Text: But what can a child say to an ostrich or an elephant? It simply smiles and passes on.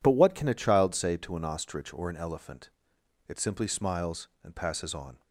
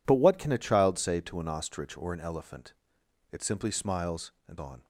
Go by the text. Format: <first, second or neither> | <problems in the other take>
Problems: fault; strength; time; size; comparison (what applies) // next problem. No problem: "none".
first | skips "passes"; at 4.5 s